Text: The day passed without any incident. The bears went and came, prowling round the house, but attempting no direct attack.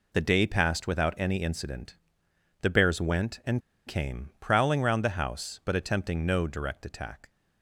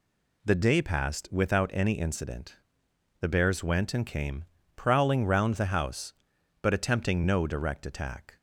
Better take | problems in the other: second | pauses between "and" and "came"; slight; at 3.6 s; 0.27 s long

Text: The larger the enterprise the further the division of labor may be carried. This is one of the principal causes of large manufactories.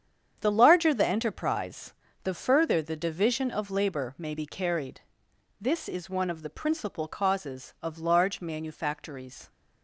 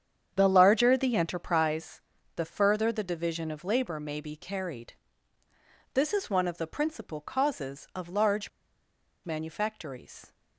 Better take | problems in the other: first | starts louder than the rest; strong; until 1.3 s; 8 dB; strong in the first // pauses between "enterprise" and "the"; slight; at 2.0 s; 0.36 s long; slight in the first // pauses between "large" and "manufactories"; noticeable; at 8.4 s; 0.75 s long

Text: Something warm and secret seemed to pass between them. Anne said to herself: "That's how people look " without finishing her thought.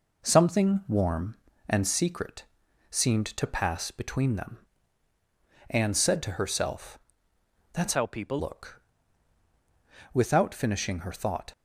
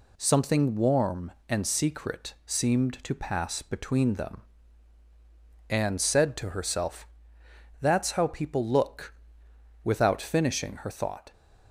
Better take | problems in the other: second | pauses between "secret" and "seemed"; noticeable; at 2.4 s; 0.48 s long // changes voice from "how" to "people"; from 7.9 to 8.3 s; 0.4 s long

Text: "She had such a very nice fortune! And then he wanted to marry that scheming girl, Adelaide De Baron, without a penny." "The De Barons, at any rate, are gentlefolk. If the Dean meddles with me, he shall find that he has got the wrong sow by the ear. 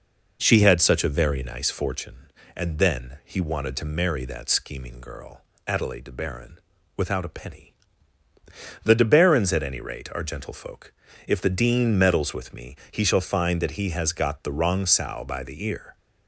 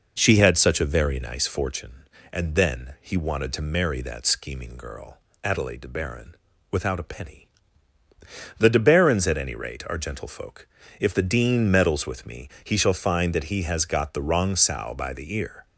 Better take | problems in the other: neither | none

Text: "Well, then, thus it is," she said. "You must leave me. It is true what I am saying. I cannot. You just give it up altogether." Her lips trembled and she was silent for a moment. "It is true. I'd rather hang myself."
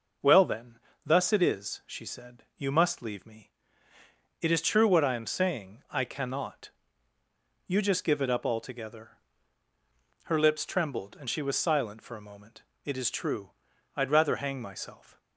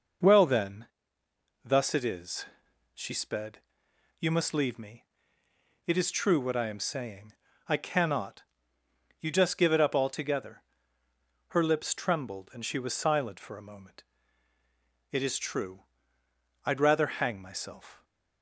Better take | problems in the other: first | says "sped" for "said"; at 3.1 s

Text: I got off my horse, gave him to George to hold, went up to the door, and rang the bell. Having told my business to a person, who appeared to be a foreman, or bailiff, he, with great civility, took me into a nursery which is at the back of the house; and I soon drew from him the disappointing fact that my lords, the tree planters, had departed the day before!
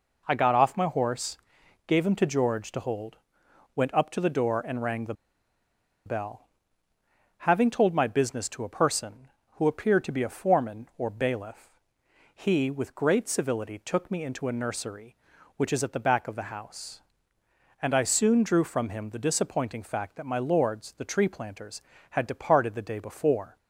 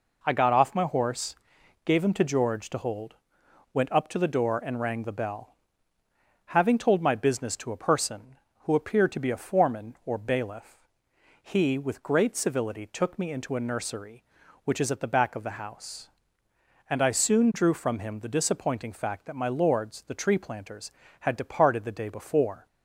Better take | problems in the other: second | pauses between "the" and "bell"; noticeable; at 5.1 s; 0.92 s long

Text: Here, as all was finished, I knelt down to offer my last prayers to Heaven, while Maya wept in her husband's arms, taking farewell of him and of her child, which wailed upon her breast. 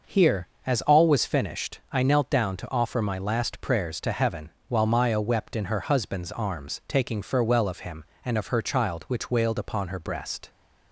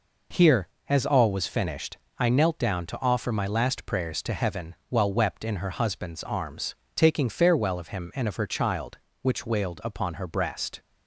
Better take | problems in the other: first | skips "Maya"; at 5.1 s

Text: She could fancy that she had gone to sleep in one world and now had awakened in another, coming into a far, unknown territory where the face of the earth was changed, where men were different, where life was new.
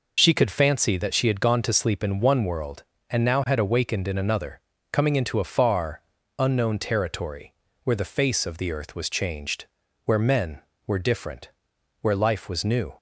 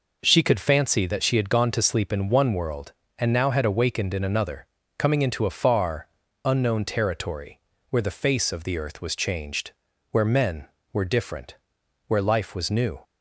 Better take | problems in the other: second | loses the start of "She"; at 0.1 s; 45 ms // pauses between "territory" and "where"; slight; at 7.5 s; 0.30 s long; slight in the second

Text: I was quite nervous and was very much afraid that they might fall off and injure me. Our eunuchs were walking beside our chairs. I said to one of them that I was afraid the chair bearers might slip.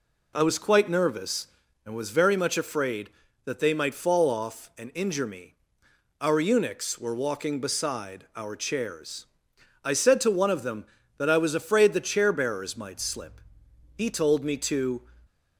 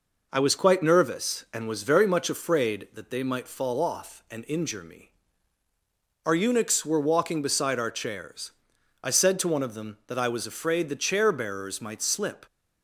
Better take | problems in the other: second | goes on to say "He told me to"; noticeable; from 13.9 s on; 1.0 s long

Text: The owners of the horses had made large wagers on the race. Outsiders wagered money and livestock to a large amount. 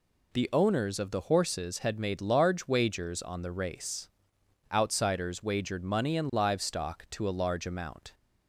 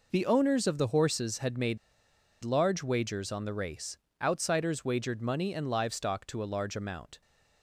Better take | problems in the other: first | pauses between "made" and "large"; noticeable; at 1.7 s; 0.64 s long

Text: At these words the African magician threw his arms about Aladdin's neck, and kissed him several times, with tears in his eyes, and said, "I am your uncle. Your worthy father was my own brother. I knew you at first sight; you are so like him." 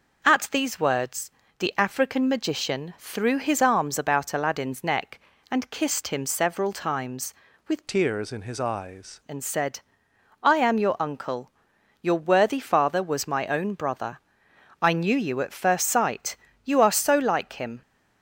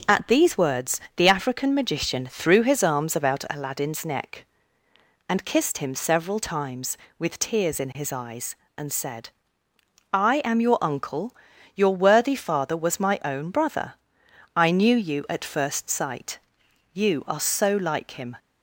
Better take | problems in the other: second | pauses between "words" and "the"; slight; at 1.3 s; 0.26 s long; slight in the second // changes voice from "tears" to "eyes"; from 7.8 to 9.1 s; 1.3 s long

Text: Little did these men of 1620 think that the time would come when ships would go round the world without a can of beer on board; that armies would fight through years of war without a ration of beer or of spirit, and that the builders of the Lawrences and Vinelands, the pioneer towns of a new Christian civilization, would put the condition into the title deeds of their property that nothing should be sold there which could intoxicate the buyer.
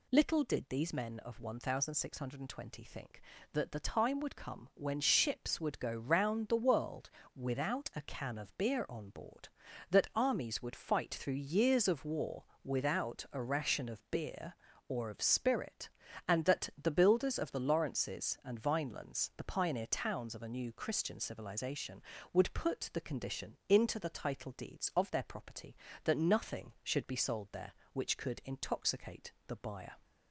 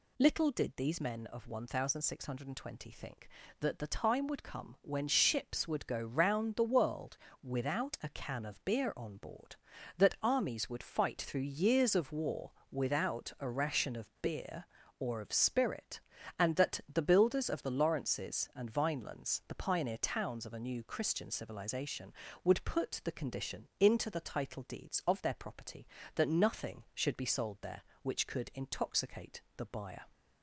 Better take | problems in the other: neither | pauses between "world" and "without"; slight; the same in both // pauses between "war" and "without"; slight; the same in both

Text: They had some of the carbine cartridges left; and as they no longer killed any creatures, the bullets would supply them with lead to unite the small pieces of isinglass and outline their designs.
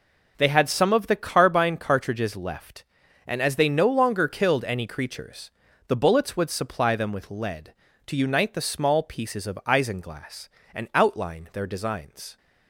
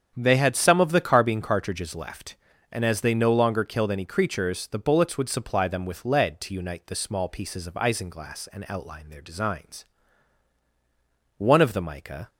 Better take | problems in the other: first | starts louder than the rest; strong; until 1.1 s; 8 dB // goes on to say "One of the mica"; noticeable; from 11.3 s on; 0.90 s long

